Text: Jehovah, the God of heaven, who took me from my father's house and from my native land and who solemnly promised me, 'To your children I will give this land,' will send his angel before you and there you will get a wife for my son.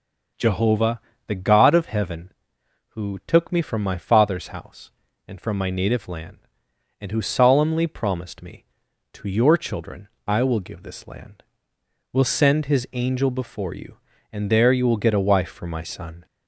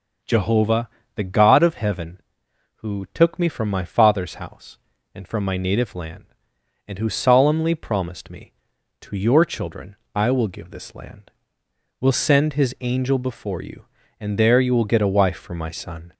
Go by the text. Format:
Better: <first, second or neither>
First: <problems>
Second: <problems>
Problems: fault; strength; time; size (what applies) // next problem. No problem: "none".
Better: neither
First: pauses between "children" and "I"; slight; at 10.0 s; 0.20 s long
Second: pauses between "children" and "I"; slight; at 9.9 s; 0.20 s long